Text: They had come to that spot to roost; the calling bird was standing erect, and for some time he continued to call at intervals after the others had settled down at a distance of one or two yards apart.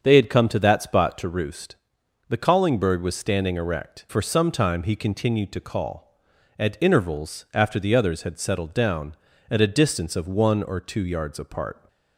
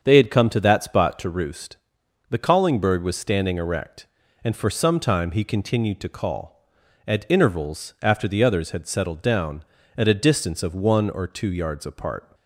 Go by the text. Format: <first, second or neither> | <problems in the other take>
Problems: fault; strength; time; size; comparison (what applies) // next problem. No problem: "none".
second | starts louder than the rest; strong; until 1.0 s; 7 dB; strong in the second // skips "and"; at 4.0 s